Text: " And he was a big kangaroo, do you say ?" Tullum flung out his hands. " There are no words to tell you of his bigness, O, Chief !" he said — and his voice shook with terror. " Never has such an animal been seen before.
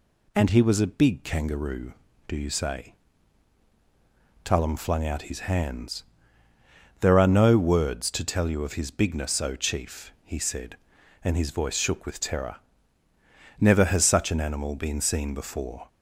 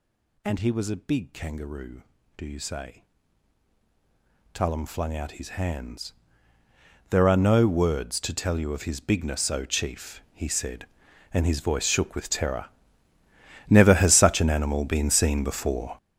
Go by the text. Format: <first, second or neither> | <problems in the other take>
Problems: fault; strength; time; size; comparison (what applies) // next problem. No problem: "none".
first | gets louder; strong; throughout; 17 dB